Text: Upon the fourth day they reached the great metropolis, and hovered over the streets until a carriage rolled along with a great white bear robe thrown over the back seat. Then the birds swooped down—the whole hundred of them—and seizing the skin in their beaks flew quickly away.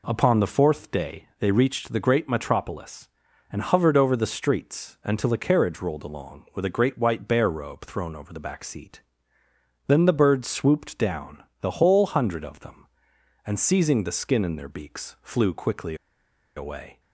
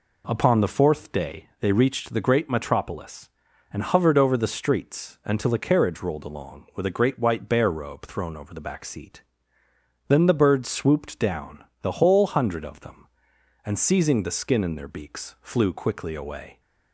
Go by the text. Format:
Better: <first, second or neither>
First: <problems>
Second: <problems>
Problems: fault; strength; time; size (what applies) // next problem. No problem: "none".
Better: second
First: pauses between "quickly" and "away"; noticeable; at 15.9 s; 0.61 s long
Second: none